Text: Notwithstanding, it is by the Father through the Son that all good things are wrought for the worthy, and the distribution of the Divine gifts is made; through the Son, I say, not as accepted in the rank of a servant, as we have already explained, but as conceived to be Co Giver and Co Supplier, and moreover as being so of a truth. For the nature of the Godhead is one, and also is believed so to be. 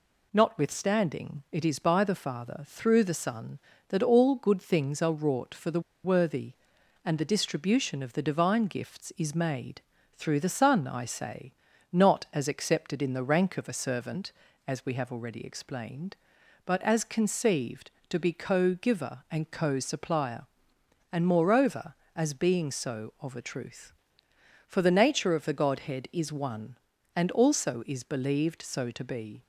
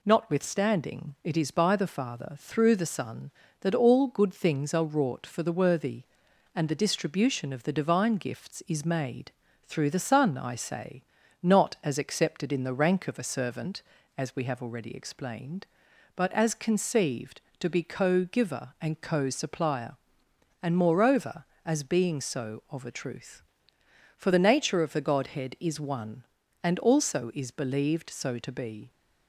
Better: second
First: pauses between "the" and "worthy"; slight; at 5.7 s; 0.24 s long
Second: none

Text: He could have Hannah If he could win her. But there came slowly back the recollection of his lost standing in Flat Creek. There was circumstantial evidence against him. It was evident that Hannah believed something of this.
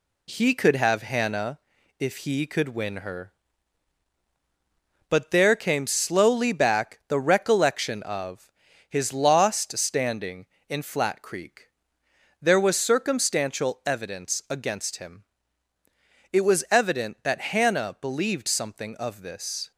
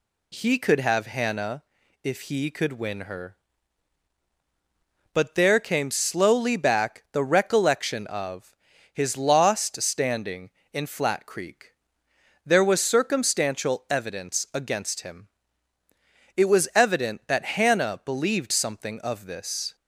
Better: second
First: gets quieter; noticeable; throughout; 4 dB // pauses between "Hannah" and "If"; at 1.5 s; 0.42 s long // pauses between "of" and "his"; slight; at 8.5 s; 0.36 s long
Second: pauses between "Hannah" and "If"; at 1.6 s; 0.42 s long // pauses between "of" and "his"; slight; at 8.5 s; 0.36 s long

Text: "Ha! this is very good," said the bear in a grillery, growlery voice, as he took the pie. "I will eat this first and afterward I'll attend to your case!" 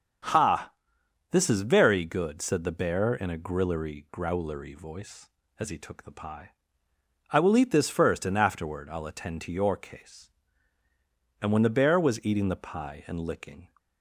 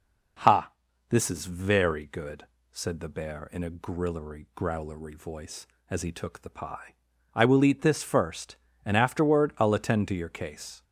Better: second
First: starts louder than the rest; strong; until 1.9 s; 7.5 dB // goes on to say "And when the bear was eating the pie and licking"; strong; from 11.4 s on; 2.2 s long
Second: none

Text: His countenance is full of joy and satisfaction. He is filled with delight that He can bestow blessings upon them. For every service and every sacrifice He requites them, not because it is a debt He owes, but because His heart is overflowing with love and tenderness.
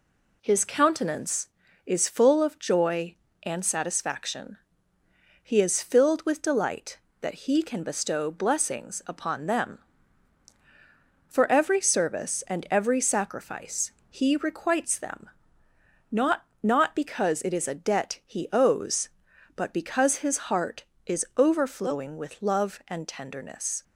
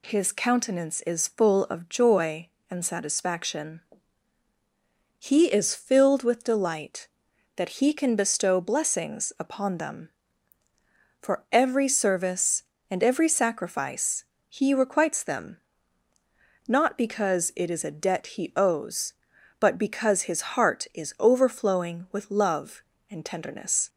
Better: second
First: pauses between "sacrifice" and "He"; slight; at 13.9 s; 0.18 s long // says "not" twice; at 16.6 s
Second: pauses between "sacrifice" and "He"; slight; at 14.2 s; 0.26 s long

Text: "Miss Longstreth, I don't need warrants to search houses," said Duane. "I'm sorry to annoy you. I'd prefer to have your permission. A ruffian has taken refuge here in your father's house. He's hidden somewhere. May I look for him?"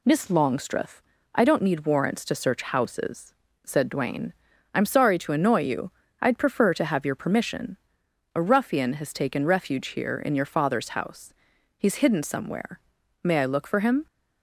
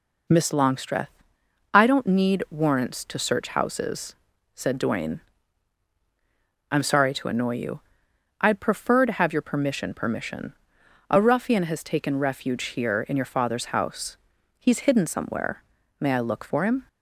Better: first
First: none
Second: says "permission" twice; at 9.9 s

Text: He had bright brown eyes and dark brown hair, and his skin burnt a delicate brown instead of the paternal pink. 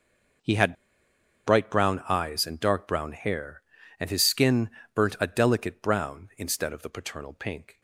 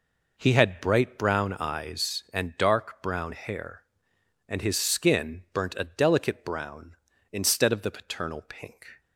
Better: second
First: starts louder than the rest; until 2.2 s; 6 dB // pauses between "had" and "bright"; noticeable; at 0.7 s; 0.72 s long // pauses between "skin" and "burnt"; slight; at 4.7 s; 0.24 s long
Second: none

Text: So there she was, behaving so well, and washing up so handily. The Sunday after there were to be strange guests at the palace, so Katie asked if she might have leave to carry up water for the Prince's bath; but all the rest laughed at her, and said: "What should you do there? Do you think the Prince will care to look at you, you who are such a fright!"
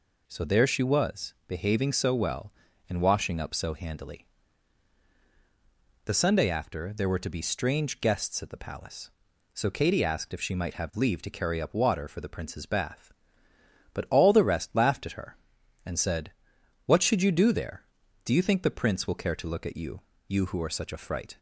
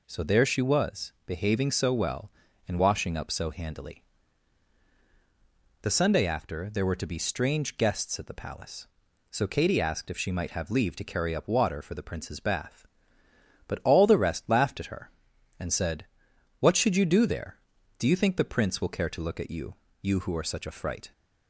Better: neither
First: none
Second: none

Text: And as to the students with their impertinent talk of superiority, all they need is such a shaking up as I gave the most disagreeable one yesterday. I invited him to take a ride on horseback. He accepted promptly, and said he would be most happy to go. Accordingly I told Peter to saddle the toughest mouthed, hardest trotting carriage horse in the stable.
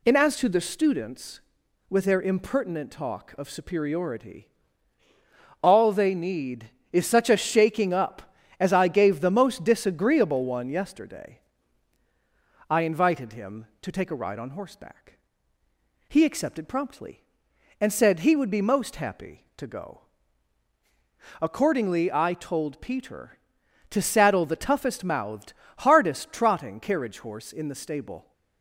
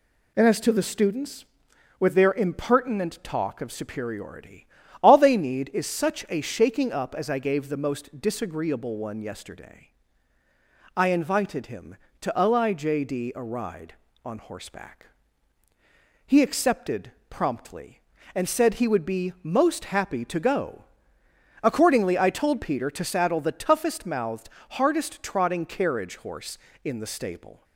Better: first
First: none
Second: says "lijd" for "take"; at 12.3 s // pauses between "accepted" and "promptly"; slight; at 17.1 s; 0.18 s long

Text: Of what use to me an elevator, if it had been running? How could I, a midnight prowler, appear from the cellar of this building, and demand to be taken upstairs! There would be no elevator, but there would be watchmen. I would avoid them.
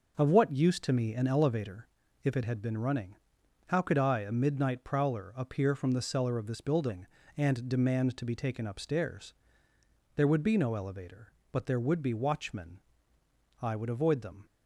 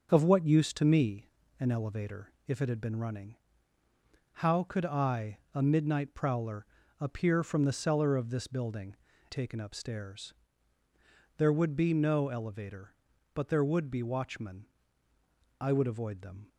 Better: first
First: none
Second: starts louder than the rest; until 1.1 s; 6.5 dB // pauses between "me" and "an"; slight; at 1.2 s; 0.32 s long // skips "and demand to be"; at 9.1 s

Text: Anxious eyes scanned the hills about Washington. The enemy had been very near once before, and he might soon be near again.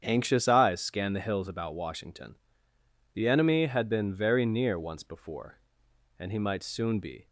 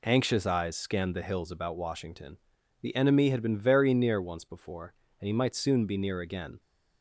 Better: second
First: starts louder than the rest; strong; until 1.0 s; 8.5 dB // stops before "near again"; at 7.2 s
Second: none

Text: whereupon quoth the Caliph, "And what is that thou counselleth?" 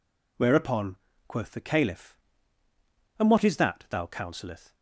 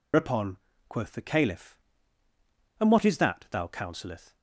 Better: first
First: pauses between "whereupon" and "quoth"; slight; at 0.9 s; 0.32 s long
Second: loses the start of "whereupon"; at 0.1 s; 165 ms // pauses between "whereupon" and "quoth"; slight; at 0.5 s; 0.32 s long

